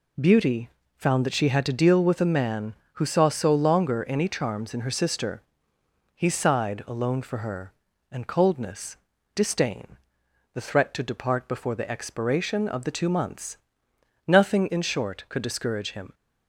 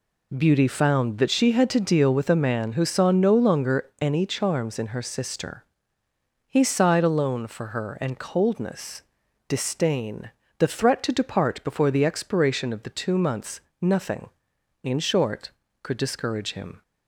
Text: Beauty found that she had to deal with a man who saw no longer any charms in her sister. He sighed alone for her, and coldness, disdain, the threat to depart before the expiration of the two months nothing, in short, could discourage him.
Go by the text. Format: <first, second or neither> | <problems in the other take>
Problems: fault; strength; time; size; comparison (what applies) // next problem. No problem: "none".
second | pauses between "Beauty" and "found"; slight; at 0.6 s; 0.30 s long // says "so" for "no"; at 3.2 s // pauses between "months" and "nothing"; noticeable; at 13.5 s; 0.70 s long; slight in the second